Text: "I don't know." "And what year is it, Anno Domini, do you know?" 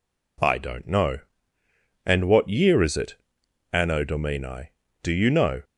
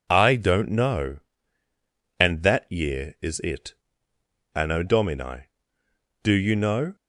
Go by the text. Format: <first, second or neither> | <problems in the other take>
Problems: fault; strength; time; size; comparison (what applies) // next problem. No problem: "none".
first | says "that" for "what"; at 2.4 s